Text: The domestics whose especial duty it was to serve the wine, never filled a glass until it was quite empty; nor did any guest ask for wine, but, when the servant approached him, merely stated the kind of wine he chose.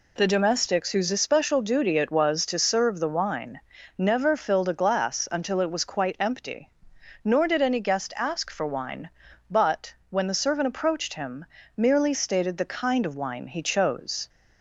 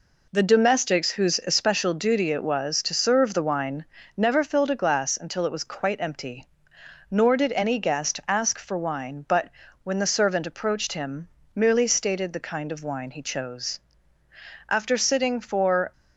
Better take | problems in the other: first | goes on to say "After sitting for"; noticeable; from 14.6 s on; 1.2 s long

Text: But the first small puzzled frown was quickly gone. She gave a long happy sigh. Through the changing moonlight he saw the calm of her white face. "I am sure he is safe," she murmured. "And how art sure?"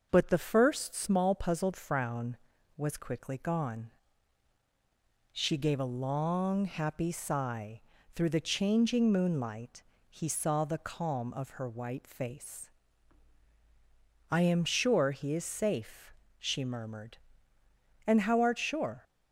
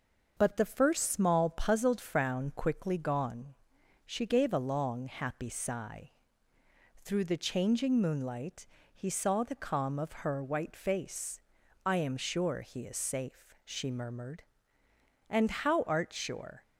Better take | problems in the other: first | starts louder than the rest; noticeable; until 1.3 s; 6 dB; noticeable in the first // skips "was"; at 2.5 s // pauses between "moonlight" and "he"; slight; at 8.6 s; 0.26 s long; slight in the first

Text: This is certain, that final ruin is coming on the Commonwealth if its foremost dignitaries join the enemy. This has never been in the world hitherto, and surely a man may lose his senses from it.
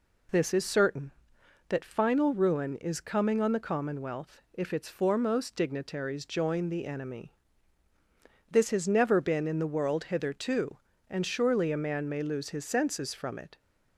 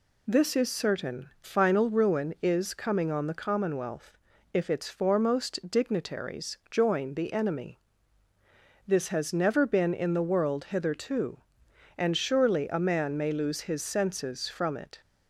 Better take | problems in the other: first | skips "that"; at 1.3 s // pauses between "Commonwealth" and "if"; slight; at 4.1 s; 0.36 s long

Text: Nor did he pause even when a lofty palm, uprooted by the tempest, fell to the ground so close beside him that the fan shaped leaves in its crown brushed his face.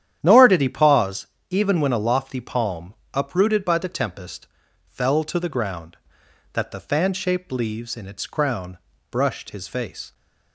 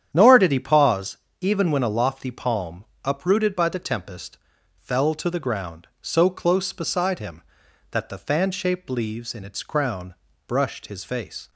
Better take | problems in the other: second | starts louder than the rest; strong; until 1.2 s; 10 dB; strong in the second // pauses between "pause" and "even"; slight; at 1.2 s; 0.22 s long; slight in the second // skips "so close beside him"; at 6.2 s // pauses between "crown" and "brushed"; slight; at 8.7 s; 0.32 s long; slight in the second

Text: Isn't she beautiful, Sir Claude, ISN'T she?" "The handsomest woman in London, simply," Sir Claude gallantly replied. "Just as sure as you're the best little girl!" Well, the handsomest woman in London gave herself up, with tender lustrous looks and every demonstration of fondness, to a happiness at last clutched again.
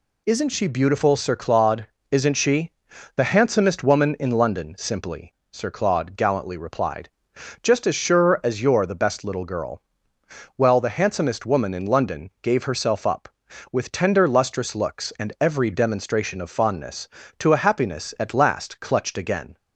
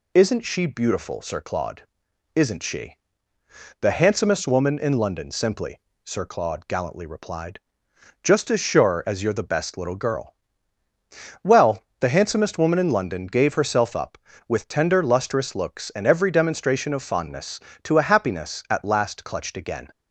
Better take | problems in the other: neither | none

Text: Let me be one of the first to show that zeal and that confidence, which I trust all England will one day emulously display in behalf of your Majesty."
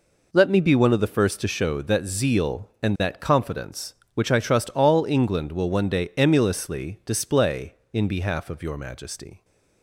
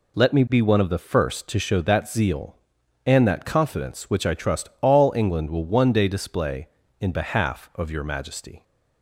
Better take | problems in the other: first | skips "emulously"; at 6.0 s

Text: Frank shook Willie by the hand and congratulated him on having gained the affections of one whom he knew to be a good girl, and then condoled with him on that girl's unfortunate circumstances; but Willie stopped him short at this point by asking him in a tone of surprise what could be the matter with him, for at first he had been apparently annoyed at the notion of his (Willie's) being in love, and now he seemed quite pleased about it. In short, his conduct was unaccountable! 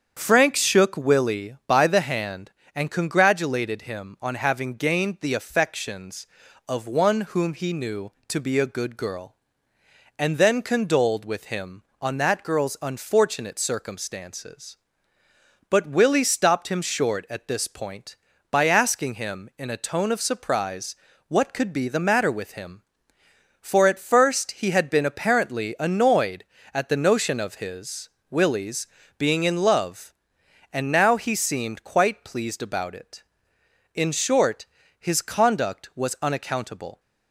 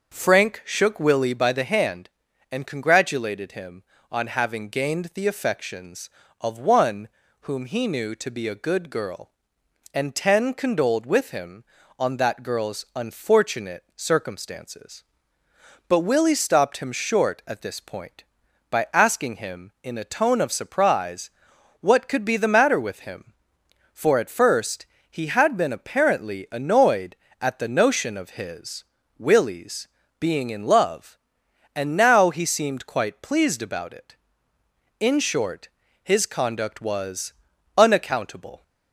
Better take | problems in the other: first | starts louder than the rest; until 1.1 s; 6.5 dB; strong in the first // pauses between "one" and "whom"; slight; at 7.0 s; 0.32 s long // says "ten" for "then"; at 10.1 s // pauses between "surprise" and "what"; noticeable; at 21.3 s; 0.50 s long; slight in the first // pauses between "first" and "he"; slight; at 24.8 s; 0.26 s long // pauses between "was" and "unaccountable"; at 37.3 s; 0.44 s long

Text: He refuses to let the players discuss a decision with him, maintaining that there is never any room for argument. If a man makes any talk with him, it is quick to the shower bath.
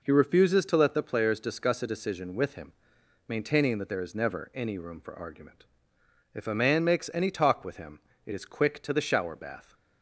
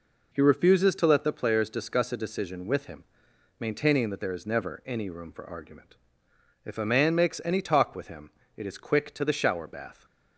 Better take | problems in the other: neither | none

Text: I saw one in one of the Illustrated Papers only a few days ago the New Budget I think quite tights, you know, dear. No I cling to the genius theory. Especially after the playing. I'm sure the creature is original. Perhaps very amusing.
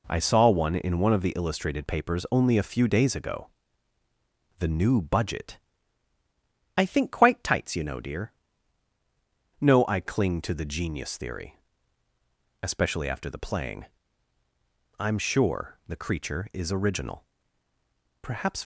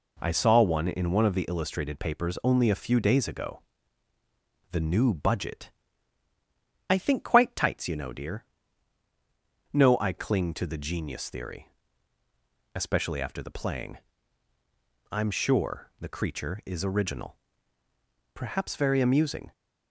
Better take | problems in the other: second | pauses between "ago" and "the"; at 3.4 s; 1.1 s long; also in the second // pauses between "Budget" and "I"; at 5.5 s; 1.2 s long; also in the second // stops before "very amusing"; at 18.5 s

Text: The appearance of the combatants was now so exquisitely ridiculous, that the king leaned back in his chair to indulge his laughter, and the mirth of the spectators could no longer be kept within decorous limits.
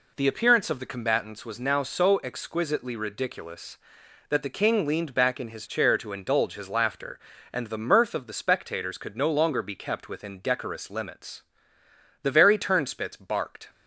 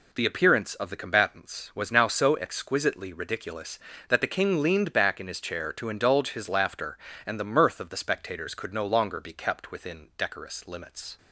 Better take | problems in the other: second | goes on to say "The very turnspits barked"; from 12.2 s on; 1.4 s long

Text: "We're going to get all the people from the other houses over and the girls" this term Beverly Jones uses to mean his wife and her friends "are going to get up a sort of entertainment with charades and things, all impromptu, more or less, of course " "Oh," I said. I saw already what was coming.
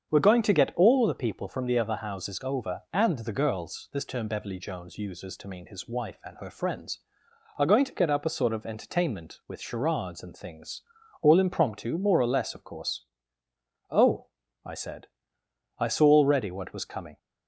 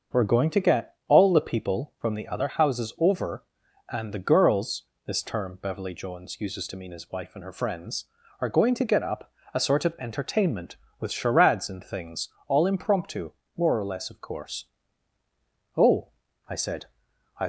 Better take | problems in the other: first | starts louder than the rest; until 1.2 s; 6.5 dB; strong in the first // pauses between "girls" and "this"; slight; at 4.8 s; 0.22 s long // pauses between "up" and "a"; slight; at 9.3 s; 0.22 s long // stops before "saw already what was coming"; at 17.4 s

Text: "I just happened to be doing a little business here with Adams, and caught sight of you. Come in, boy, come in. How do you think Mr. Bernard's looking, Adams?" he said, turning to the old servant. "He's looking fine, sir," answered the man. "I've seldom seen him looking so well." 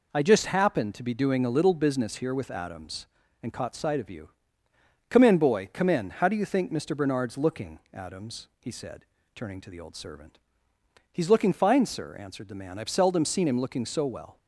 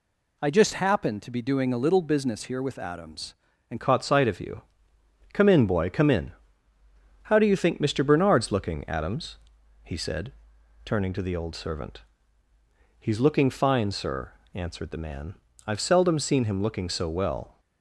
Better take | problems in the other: first | changes voice at "caught"; from 3.8 s on; 13.7 s long

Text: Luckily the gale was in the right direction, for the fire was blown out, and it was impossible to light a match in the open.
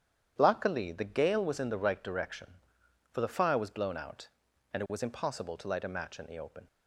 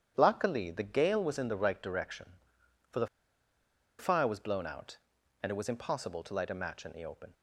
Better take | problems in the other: first | starts louder than the rest; strong; until 1.1 s; 9.5 dB; strong in the first // pauses between "the" and "fire"; noticeable; at 3.0 s; 0.92 s long

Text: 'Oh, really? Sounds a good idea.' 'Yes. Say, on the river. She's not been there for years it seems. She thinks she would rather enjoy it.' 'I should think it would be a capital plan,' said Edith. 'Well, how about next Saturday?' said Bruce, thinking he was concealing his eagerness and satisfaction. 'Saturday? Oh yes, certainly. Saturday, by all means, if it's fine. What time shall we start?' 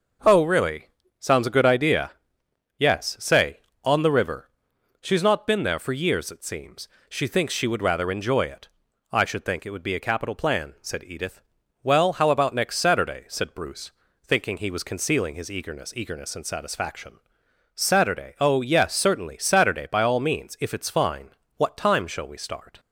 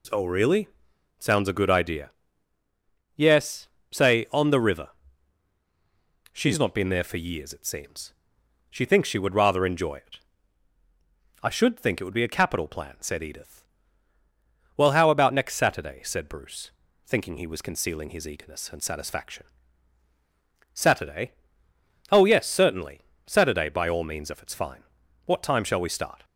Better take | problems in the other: second | says "eagerness" twice; at 15.9 s

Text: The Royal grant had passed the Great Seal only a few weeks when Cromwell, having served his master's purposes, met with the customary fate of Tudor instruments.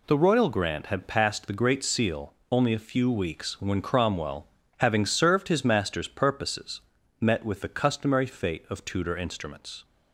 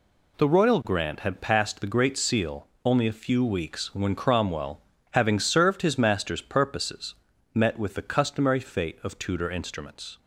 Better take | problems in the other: neither | pauses between "Seal" and "only"; slight; the same in both

